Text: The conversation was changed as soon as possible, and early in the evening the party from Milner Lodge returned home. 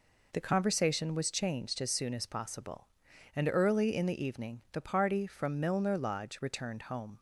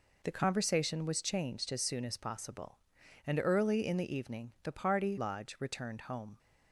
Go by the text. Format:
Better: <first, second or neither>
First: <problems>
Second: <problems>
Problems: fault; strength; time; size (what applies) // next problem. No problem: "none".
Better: first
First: none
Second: skips "from Milner"; at 5.1 s